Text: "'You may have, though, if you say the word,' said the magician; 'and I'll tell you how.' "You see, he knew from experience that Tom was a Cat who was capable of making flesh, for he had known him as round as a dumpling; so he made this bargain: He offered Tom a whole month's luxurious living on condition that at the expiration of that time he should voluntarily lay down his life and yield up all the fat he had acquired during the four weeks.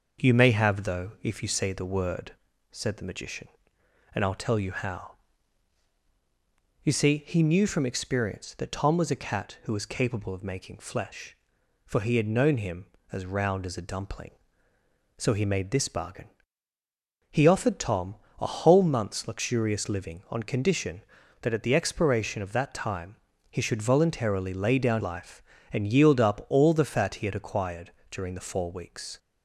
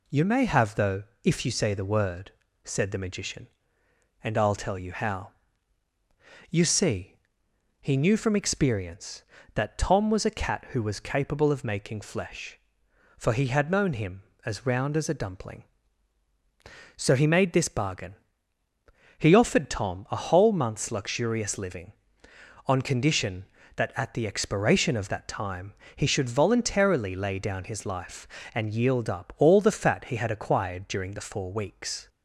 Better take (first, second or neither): second